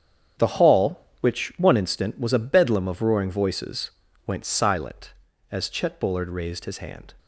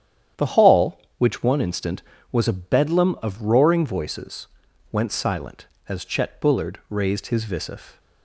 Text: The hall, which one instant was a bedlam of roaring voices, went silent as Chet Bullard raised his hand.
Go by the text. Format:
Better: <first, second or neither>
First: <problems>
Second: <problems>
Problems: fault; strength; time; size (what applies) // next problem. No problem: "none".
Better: first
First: starts louder than the rest; strong; until 1.6 s; 8.5 dB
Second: starts louder than the rest; strong; until 1.5 s; 10 dB // says "visif" for "hand"; at 7.4 s